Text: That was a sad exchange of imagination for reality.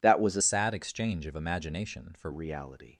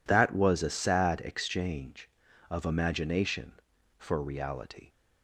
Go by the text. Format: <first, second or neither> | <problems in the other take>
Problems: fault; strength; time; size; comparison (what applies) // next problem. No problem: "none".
second | changes voice from "sad" to "for"; from 0.4 to 2.3 s; 1.9 s long